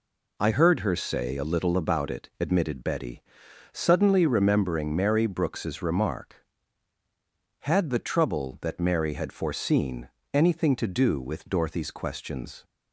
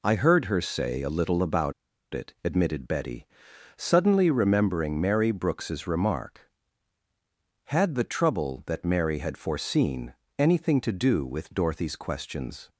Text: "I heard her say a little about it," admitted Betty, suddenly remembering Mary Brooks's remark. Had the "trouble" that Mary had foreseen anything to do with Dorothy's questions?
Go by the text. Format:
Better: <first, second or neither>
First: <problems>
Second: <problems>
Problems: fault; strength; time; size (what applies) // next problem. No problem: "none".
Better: first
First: pauses between "foreseen" and "anything"; slight; at 10.0 s; 0.24 s long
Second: pauses between "about" and "it"; at 1.7 s; 0.40 s long // pauses between "foreseen" and "anything"; slight; at 10.1 s; 0.24 s long